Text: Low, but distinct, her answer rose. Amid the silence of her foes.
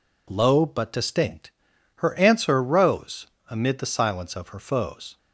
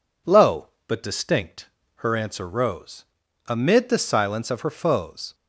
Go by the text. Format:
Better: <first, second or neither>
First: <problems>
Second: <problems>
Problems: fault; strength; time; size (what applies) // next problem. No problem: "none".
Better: neither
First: none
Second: none